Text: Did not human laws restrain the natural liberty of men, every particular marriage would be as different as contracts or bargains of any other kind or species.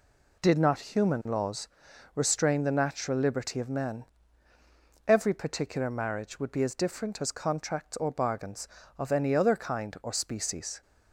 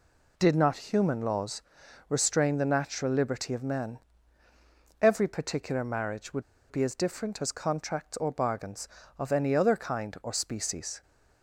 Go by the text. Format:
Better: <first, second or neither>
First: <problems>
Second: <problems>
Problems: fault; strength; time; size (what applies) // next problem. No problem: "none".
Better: first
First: pauses between "laws" and "restrain"; noticeable; at 1.6 s; 0.48 s long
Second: pauses between "laws" and "restrain"; noticeable; at 1.6 s; 0.48 s long // pauses between "would" and "be"; slight; at 6.4 s; 0.26 s long